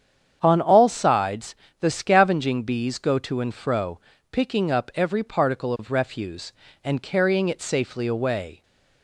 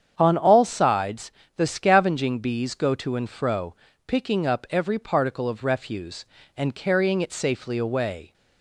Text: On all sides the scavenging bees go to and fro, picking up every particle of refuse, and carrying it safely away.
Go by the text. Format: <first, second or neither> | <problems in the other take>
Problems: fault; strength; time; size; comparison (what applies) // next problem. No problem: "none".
neither | starts louder than the rest; strong; the same in both // pauses between "sides" and "the"; slight; the same in both